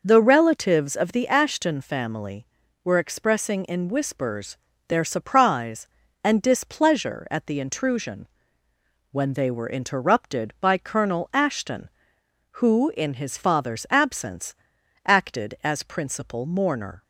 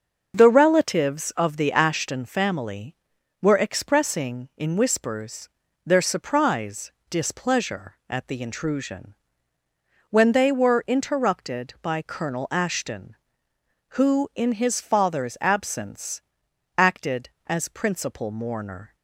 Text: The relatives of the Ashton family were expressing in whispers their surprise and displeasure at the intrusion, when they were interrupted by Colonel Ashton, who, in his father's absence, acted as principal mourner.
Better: first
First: pauses between "whispers" and "their"; slight; at 4.5 s; 0.32 s long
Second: starts louder than the rest; until 1.4 s; 6.5 dB // pauses between "whispers" and "their"; at 5.4 s; 0.38 s long // skips "and"; at 7.0 s

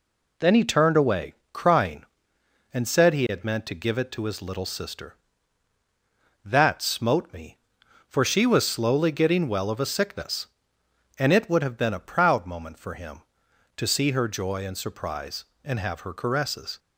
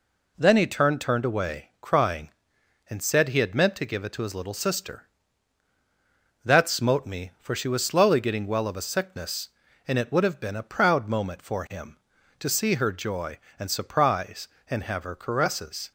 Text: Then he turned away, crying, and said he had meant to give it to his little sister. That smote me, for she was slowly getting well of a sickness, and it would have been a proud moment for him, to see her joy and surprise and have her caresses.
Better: first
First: none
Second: says "turned" twice; at 1.0 s

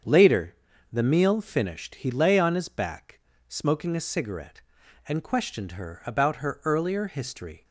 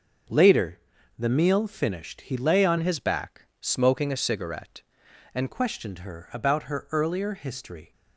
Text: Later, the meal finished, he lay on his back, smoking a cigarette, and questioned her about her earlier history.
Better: first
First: starts louder than the rest; strong; until 1.4 s; 7.5 dB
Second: starts louder than the rest; until 1.7 s; 6.5 dB // changes voice from "his" to "and"; from 2.8 to 5.4 s; 2.6 s long

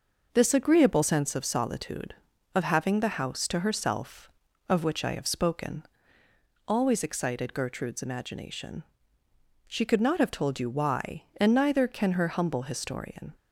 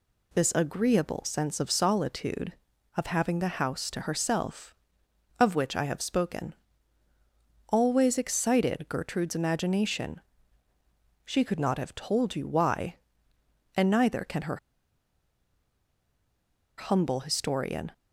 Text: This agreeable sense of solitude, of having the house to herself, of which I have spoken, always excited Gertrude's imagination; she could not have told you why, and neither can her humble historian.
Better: first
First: none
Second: pauses between "her" and "humble"; strong; at 14.5 s; 2.2 s long

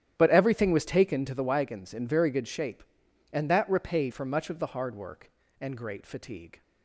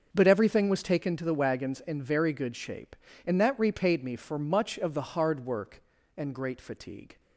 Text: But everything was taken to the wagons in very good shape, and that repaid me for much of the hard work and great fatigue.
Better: second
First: starts louder than the rest; strong; until 1.1 s; 10.5 dB // skips "me"; at 4.1 s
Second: starts louder than the rest; until 1.1 s; 6.5 dB

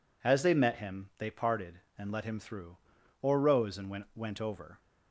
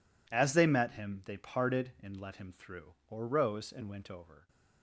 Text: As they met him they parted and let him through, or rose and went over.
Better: second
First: says "went" twice; at 4.1 s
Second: none

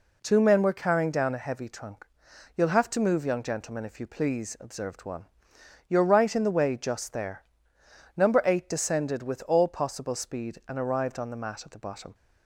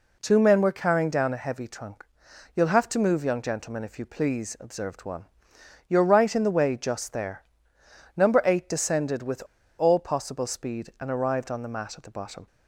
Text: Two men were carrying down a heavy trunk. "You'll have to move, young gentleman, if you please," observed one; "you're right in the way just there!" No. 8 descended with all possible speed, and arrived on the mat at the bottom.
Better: first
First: none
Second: pauses between "with" and "all"; slight; at 9.4 s; 0.35 s long

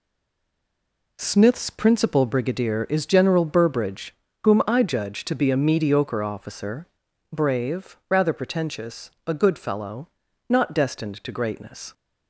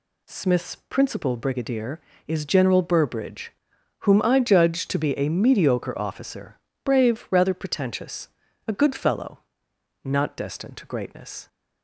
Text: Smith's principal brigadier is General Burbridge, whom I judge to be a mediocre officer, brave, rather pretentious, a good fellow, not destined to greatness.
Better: second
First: stays silent before the first word; noticeable; until 1.1 s; 1.1 s long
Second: none

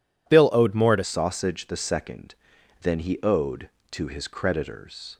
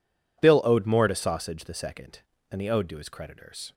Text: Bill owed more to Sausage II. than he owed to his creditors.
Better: second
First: changes voice at "Sausage"; from 1.0 s on; 4.1 s long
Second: none

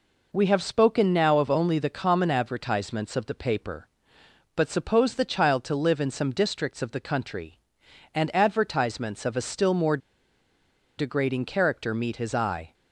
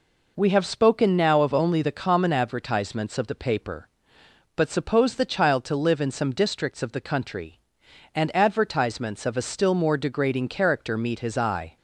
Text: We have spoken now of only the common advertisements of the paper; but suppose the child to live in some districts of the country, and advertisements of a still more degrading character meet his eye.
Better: second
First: pauses between "more" and "degrading"; at 9.9 s; 1.0 s long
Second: none

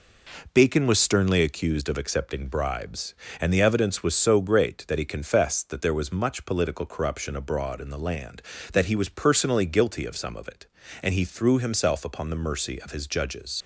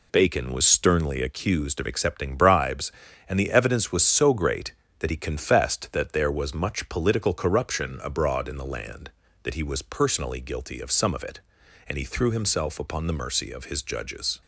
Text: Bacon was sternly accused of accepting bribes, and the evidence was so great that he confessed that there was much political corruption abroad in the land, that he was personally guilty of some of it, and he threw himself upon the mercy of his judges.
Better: second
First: leaves "judges" unfinished; at 13.6 s; 70 ms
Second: none

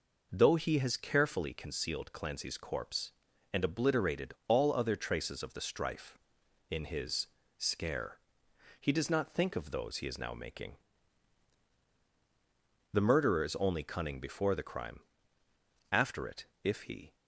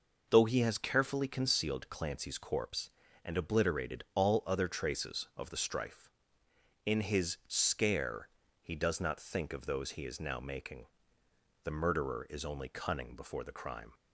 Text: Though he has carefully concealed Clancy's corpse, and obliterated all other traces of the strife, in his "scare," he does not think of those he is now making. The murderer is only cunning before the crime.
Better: second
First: pauses between "his" and "scare"; slight; at 7.2 s; 0.30 s long // goes on to say "After it if he"; noticeable; from 15.9 s on; 1.2 s long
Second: none

